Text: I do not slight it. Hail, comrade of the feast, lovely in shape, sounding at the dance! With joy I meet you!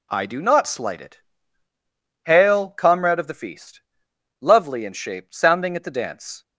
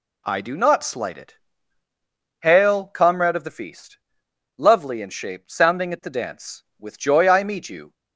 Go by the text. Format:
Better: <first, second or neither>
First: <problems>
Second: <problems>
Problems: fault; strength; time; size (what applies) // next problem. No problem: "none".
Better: second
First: stops before "With joy I meet you"; at 6.4 s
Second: none